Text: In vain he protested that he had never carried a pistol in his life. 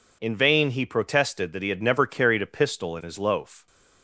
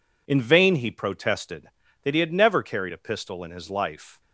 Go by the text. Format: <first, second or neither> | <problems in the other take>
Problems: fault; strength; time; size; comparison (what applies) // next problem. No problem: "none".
second | says "loaf" for "life"; at 3.1 s